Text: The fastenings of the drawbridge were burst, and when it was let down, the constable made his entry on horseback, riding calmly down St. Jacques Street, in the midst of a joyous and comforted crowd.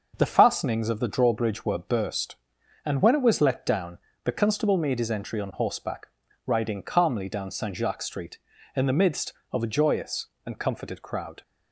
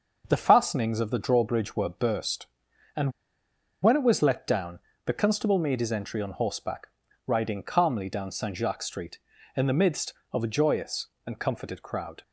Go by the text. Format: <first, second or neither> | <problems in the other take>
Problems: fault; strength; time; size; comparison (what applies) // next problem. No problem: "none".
first | pauses between "and" and "when"; noticeable; at 3.1 s; 0.70 s long